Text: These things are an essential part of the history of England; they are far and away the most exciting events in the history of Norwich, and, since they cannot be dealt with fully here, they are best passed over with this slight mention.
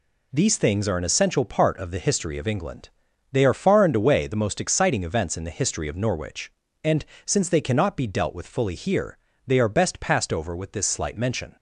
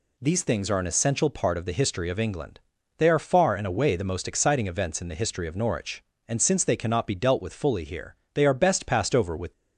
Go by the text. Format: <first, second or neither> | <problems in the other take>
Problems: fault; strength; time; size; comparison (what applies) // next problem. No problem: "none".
first | stops before "this slight mention"; at 9.5 s